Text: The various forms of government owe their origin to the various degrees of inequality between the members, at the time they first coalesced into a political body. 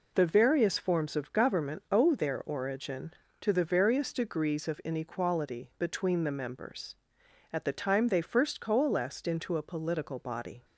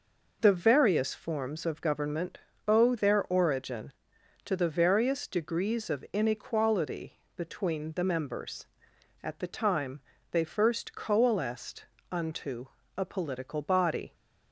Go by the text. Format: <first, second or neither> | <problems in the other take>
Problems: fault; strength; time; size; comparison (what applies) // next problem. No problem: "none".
first | pauses between "government" and "owe"; slight; at 2.3 s; 0.30 s long // pauses between "inequality" and "between"; slight; at 7.1 s; 0.18 s long // pauses between "time" and "they"; slight; at 9.9 s; 0.30 s long // says "unto" for "into"; at 12.1 s